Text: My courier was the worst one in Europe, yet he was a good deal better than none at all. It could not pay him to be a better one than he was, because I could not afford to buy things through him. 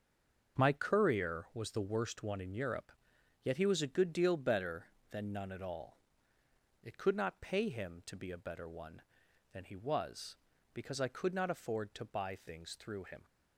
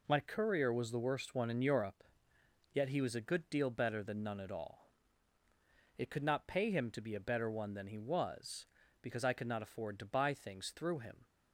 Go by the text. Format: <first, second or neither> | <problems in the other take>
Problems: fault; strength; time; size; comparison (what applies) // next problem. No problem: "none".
second | stays silent before the first word; slight; until 0.5 s; 0.5 s long // starts louder than the rest; until 1.6 s; 6.5 dB